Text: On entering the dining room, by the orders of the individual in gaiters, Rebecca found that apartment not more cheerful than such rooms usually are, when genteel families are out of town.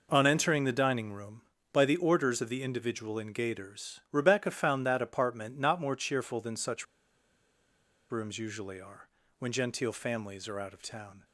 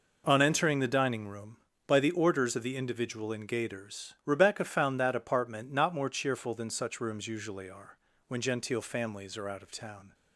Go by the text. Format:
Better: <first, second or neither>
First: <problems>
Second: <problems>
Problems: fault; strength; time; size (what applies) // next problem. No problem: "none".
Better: second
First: pauses between "such" and "rooms"; strong; at 6.8 s; 1.2 s long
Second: none